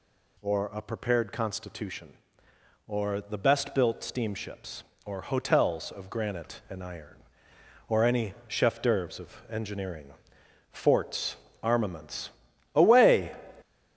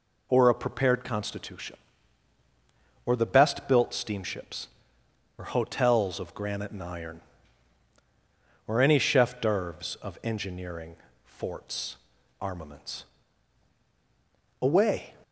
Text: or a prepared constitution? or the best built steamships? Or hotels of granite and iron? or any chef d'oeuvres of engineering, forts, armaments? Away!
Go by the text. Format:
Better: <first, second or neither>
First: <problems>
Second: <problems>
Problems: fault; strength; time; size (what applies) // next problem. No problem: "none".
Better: second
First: gets louder; noticeable; throughout; 5.5 dB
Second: none